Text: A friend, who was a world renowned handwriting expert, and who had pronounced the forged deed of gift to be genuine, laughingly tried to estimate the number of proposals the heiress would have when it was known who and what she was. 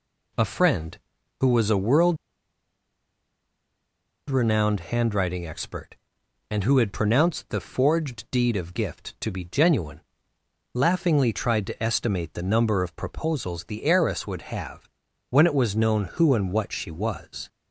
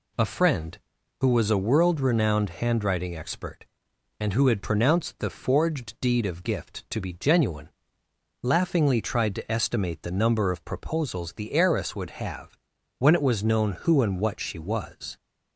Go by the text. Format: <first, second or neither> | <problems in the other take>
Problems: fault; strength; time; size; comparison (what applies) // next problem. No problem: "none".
second | pauses between "world" and "renowned"; strong; at 2.1 s; 2.1 s long // pauses between "have" and "when"; at 14.8 s; 0.40 s long; also in the second